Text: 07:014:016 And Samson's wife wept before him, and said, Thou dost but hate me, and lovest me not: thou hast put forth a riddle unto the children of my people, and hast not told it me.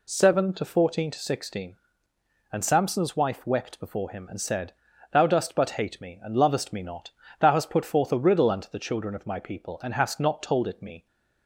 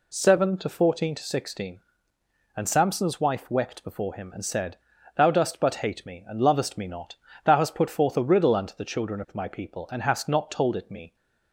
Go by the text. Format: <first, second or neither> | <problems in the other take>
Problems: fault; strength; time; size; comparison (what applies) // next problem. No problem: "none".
neither | none